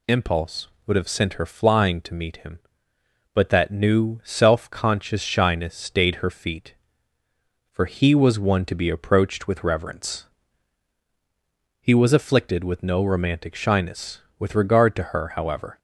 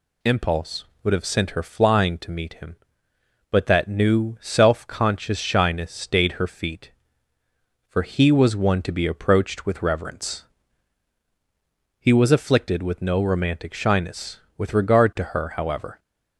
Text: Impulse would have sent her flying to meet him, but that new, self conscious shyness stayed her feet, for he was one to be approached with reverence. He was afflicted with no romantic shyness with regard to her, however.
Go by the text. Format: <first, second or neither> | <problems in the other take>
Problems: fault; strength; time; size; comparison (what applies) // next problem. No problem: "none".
neither | none